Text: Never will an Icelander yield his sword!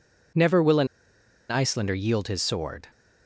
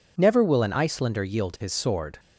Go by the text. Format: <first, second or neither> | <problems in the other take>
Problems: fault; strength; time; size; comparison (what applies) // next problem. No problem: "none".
second | pauses between "an" and "Icelander"; noticeable; at 0.8 s; 0.63 s long